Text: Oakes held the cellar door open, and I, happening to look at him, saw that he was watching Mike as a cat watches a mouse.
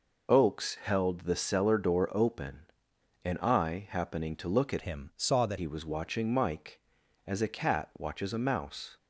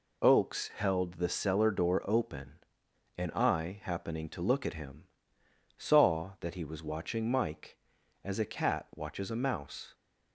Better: second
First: changes voice from "him" to "that"; from 4.8 to 5.5 s; 0.7 s long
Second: none

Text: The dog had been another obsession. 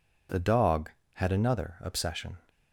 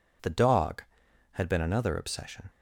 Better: second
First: skips "been"; at 1.3 s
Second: none

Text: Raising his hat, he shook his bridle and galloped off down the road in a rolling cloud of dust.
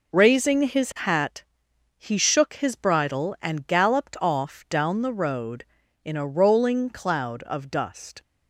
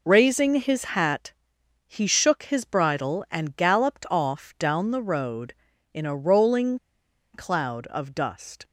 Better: first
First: none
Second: pauses between "rolling" and "cloud"; noticeable; at 6.7 s; 0.55 s long

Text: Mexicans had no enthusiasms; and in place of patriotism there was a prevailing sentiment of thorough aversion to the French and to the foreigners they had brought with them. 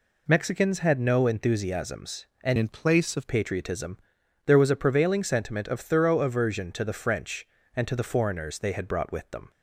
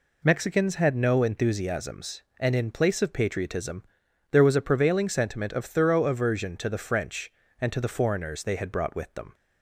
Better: second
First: changes voice from "in" to "of"; from 2.5 to 3.2 s; 0.7 s long // pauses between "patriotism" and "there"; noticeable; at 3.9 s; 0.48 s long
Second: pauses between "patriotism" and "there"; noticeable; at 3.8 s; 0.48 s long

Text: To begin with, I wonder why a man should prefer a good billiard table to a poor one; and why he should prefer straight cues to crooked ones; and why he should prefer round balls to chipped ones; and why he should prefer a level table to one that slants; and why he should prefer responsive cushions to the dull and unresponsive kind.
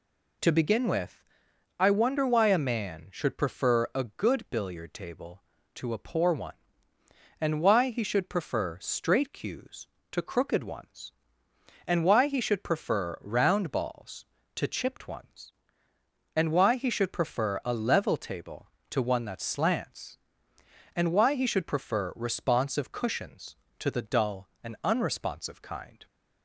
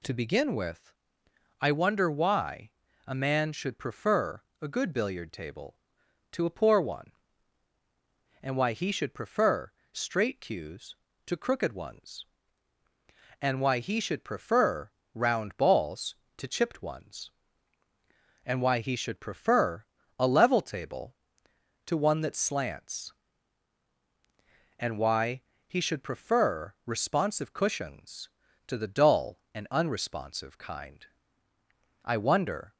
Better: first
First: none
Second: pauses between "why" and "a"; slight; at 2.7 s; 0.36 s long // pauses between "prefer" and "a"; slight; at 4.4 s; 0.20 s long // pauses between "prefer" and "straight"; slight; at 9.7 s; 0.22 s long // pauses between "prefer" and "round"; slight; at 14.9 s; 0.24 s long // pauses between "prefer" and "a"; slight; at 19.8 s; 0.34 s long // pauses between "why" and "he"; slight; at 25.4 s; 0.26 s long // goes on to say "I wonder"; noticeable; from 32.0 s on; 0.70 s long

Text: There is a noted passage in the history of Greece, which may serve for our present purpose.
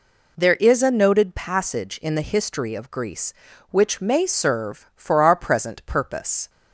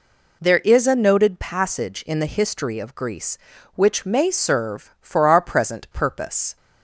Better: neither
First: none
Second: none

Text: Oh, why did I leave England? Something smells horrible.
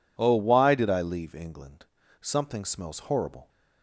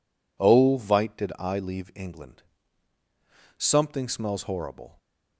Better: first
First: none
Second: says "vite" for "why"; at 0.7 s

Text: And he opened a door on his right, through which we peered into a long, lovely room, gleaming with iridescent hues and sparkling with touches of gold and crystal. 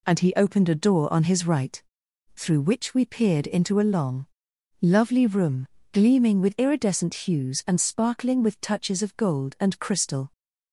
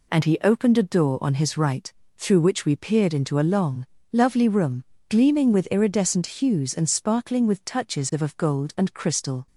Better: first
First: none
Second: says "of" twice; at 8.2 s

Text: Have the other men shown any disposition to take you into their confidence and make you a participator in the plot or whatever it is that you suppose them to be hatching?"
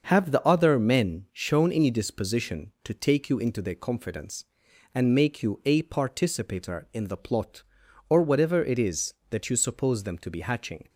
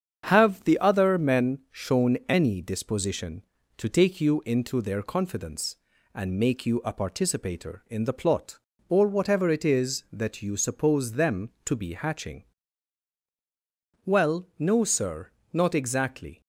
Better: first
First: starts louder than the rest; until 1.0 s; 6.5 dB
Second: starts louder than the rest; strong; until 1.2 s; 7.5 dB // goes on to say "Well no sir not exactly"; strong; from 14.0 s on; 2.3 s long

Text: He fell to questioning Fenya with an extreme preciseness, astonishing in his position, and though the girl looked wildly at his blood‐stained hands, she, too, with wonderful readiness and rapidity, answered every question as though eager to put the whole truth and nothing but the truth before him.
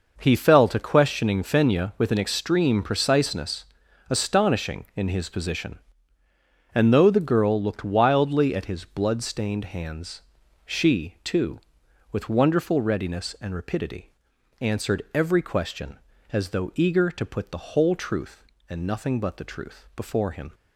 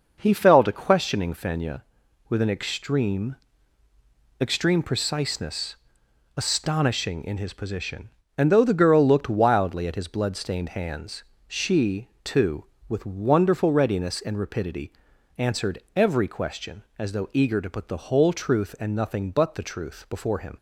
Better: first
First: none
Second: says "extreme" twice; at 4.4 s

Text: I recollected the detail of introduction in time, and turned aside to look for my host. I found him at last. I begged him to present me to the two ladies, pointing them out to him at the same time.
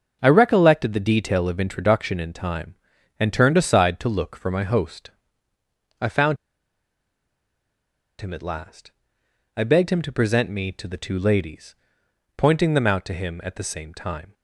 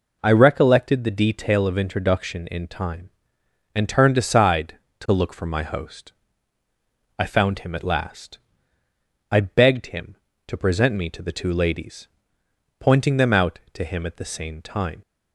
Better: second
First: starts louder than the rest; until 1.2 s; 6.5 dB // pauses between "found" and "him"; strong; at 6.3 s; 1.8 s long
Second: none

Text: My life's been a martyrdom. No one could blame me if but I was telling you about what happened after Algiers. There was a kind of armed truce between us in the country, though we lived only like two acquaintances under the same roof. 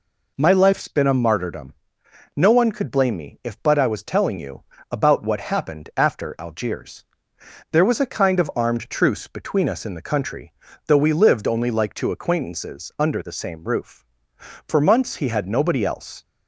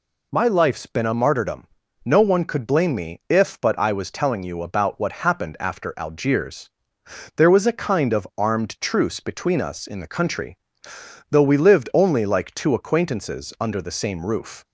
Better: second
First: pauses between "you" and "about"; slight; at 4.6 s; 0.26 s long // goes on to say "For months he had nobody else"; from 14.6 s on; 1.5 s long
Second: none

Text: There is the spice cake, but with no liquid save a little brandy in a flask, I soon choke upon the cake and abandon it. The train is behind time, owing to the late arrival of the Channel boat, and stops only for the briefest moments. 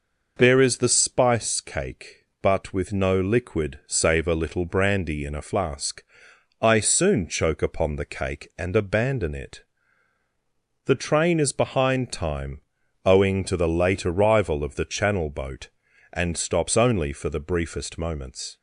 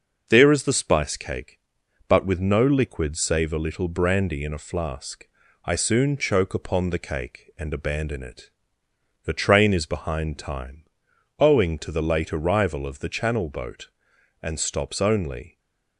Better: first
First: none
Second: stays silent after the last word; slight; from 15.4 s on; 0.5 s long // stops before "for the briefest moments"; at 15.5 s

